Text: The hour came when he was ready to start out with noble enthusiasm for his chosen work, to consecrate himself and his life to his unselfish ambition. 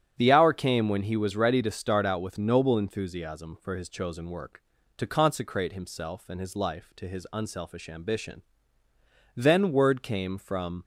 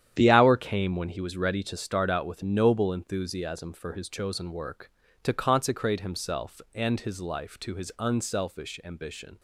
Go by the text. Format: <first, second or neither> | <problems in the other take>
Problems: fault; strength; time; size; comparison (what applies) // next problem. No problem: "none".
second | starts louder than the rest; strong; until 1.2 s; 8.5 dB; strong in the second // goes on to say "Then word came from"; from 9.3 s on; 1.5 s long